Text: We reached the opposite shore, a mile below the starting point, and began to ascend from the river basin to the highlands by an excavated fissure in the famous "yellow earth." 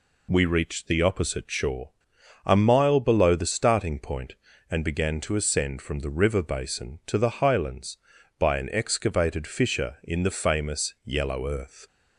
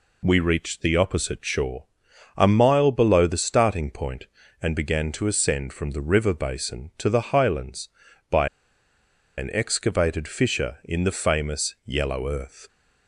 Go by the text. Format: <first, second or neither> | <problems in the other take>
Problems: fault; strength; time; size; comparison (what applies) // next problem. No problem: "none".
first | pauses between "by" and "an"; noticeable; at 8.4 s; 0.89 s long